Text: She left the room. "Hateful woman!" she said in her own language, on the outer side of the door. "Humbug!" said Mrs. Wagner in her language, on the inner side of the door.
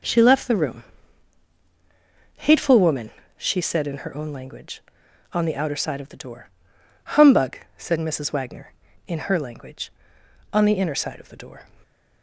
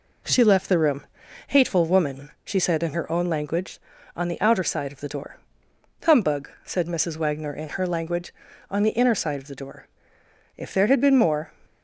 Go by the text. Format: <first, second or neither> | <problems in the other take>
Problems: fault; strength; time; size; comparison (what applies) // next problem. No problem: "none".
first | goes on to say "If there had been more"; noticeable; from 10.5 s on; 0.96 s long